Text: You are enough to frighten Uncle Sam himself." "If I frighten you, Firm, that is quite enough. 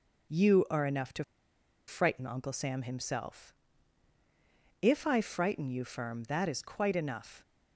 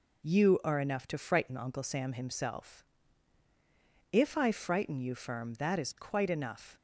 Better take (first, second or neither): second